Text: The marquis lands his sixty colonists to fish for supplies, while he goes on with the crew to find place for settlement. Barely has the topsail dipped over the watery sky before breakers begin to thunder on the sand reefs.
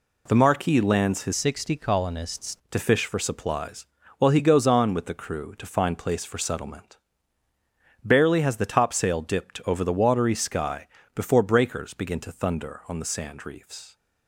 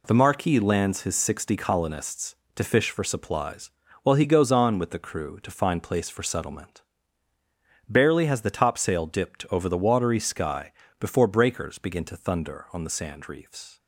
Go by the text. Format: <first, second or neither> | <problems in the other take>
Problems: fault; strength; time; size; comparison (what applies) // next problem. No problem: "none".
second | changes voice from "sixty" to "colonists"; from 1.3 to 2.5 s; 1.2 s long // pauses between "sky" and "before"; slight; at 10.8 s; 0.28 s long; slight in the second